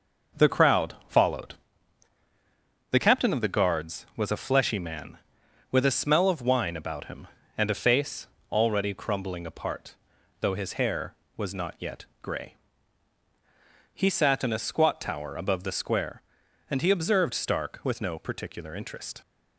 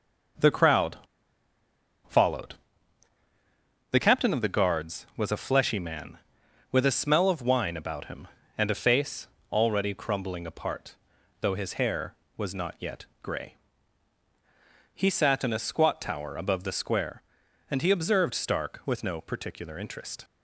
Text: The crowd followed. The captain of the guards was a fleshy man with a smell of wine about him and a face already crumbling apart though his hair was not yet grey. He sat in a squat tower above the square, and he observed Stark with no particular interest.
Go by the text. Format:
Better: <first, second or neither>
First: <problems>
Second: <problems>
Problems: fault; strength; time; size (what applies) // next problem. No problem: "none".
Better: first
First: pauses between "face" and "already"; slight; at 8.2 s; 0.24 s long // pauses between "apart" and "though"; noticeable; at 9.9 s; 0.46 s long // pauses between "yet" and "grey"; slight; at 12.0 s; 0.18 s long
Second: pauses between "crowd" and "followed"; at 0.9 s; 1.0 s long // pauses between "face" and "already"; slight; at 9.2 s; 0.24 s long // pauses between "apart" and "though"; noticeable; at 10.9 s; 0.46 s long // pauses between "yet" and "grey"; slight; at 13.0 s; 0.18 s long